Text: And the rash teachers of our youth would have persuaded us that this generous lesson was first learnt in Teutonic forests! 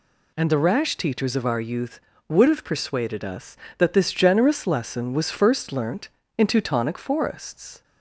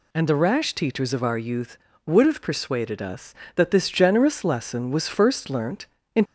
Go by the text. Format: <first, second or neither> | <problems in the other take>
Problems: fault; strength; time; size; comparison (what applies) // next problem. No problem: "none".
first | stops before "Teutonic forests"; at 6.2 s